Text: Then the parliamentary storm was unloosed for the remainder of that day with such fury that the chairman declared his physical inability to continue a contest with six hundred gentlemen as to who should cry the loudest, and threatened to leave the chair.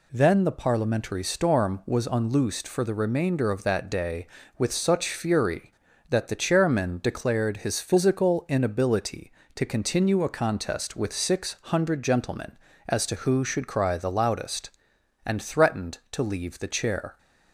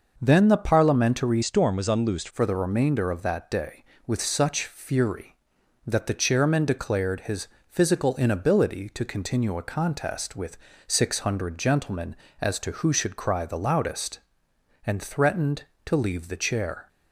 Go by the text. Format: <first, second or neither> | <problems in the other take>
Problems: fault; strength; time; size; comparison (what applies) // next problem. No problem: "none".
first | changes voice from "storm" to "unloosed"; from 1.4 to 2.2 s; 0.8 s long // pauses between "his" and "physical"; slight; at 7.4 s; 0.22 s long // pauses between "with" and "six"; slight; at 10.5 s; 0.32 s long